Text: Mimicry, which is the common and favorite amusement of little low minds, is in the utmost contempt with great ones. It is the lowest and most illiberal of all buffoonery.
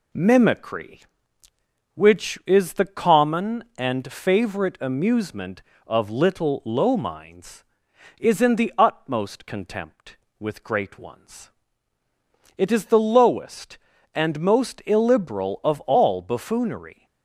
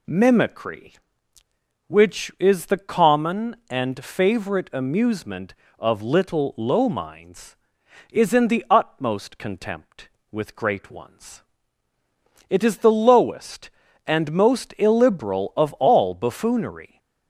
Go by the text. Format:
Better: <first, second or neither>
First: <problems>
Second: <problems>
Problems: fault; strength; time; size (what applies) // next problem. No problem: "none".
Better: second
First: gets quieter; slight; throughout; 3.5 dB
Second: none